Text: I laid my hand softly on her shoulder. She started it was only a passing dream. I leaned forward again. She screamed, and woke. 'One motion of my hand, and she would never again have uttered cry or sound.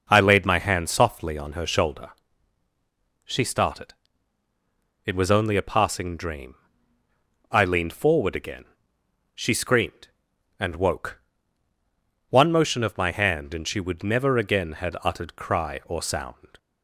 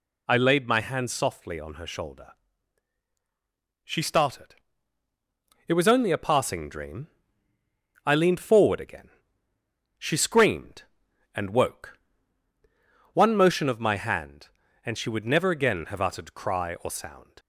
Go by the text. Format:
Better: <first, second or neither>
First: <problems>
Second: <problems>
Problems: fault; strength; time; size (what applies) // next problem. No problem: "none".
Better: second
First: pauses between "started" and "it"; at 3.9 s; 1.1 s long // says "had" for "have"; at 14.7 s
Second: pauses between "started" and "it"; at 4.5 s; 1.1 s long